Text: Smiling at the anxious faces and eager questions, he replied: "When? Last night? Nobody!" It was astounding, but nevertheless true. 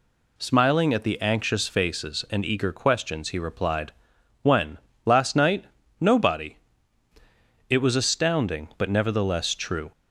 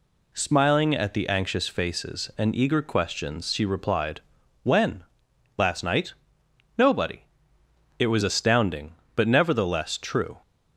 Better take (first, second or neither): first